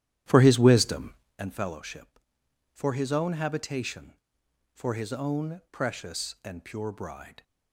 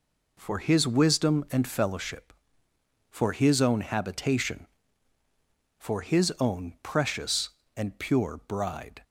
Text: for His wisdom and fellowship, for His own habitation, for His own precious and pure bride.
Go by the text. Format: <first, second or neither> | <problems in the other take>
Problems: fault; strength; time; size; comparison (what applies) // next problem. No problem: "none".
second | starts louder than the rest; strong; until 1.4 s; 12 dB